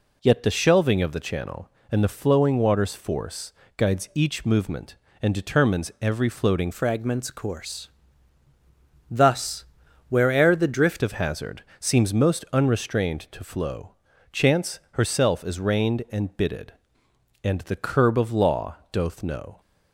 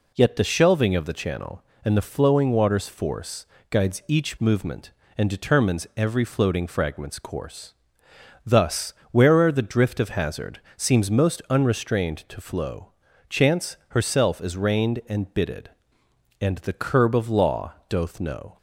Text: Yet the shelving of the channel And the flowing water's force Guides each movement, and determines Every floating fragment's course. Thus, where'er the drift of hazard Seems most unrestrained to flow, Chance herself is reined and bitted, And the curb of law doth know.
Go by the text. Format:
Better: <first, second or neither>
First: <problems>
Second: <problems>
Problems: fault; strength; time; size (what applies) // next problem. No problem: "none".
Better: second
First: pauses between "force" and "Guides"; slight; at 3.5 s; 0.26 s long // changes voice from "fragment's" to "drift"; from 6.7 to 11.0 s; 4.3 s long // pauses between "hazard" and "Seems"; slight; at 11.6 s; 0.16 s long // pauses between "law" and "doth"; slight; at 18.7 s; 0.16 s long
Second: pauses between "force" and "Guides"; slight; at 3.4 s; 0.26 s long // pauses between "hazard" and "Seems"; slight; at 10.6 s; 0.16 s long // pauses between "law" and "doth"; slight; at 17.7 s; 0.16 s long